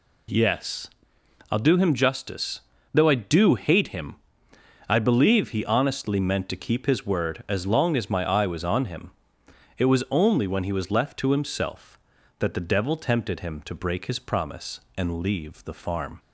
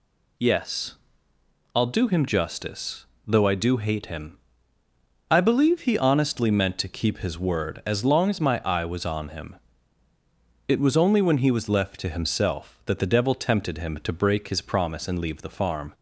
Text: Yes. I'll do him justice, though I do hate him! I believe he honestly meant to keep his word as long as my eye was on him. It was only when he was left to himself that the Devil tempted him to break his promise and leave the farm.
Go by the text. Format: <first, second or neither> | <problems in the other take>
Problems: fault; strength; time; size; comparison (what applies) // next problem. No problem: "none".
neither | none